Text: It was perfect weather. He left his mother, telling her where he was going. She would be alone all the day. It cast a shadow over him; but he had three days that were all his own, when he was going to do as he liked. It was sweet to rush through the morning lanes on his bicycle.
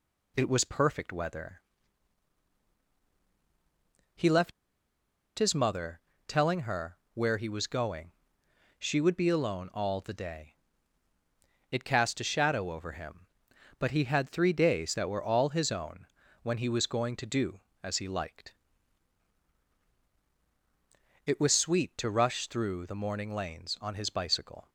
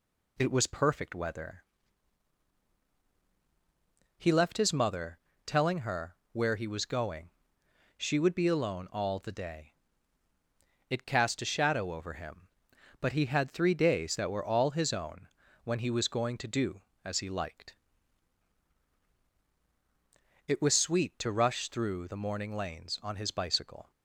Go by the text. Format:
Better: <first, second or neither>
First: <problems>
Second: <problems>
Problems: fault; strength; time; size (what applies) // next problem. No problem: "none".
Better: second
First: pauses between "left" and "his"; noticeable; at 4.5 s; 0.86 s long // pauses between "her" and "where"; slight; at 6.9 s; 0.16 s long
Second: pauses between "her" and "where"; slight; at 6.1 s; 0.16 s long